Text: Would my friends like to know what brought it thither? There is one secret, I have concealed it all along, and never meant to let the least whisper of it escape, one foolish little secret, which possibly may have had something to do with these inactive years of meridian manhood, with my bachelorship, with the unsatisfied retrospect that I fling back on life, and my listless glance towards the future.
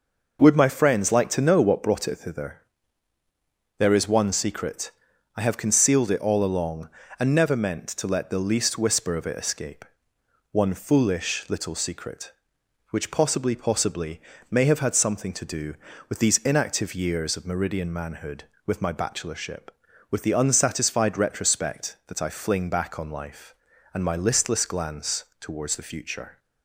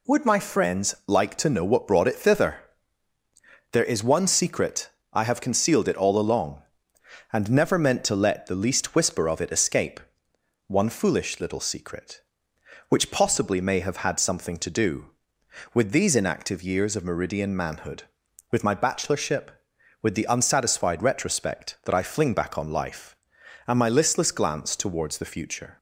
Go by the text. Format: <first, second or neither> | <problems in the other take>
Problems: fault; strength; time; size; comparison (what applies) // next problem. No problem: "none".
second | says "possibly" twice; at 13.5 s // pauses between "glance" and "towards"; slight; at 25.2 s; 0.16 s long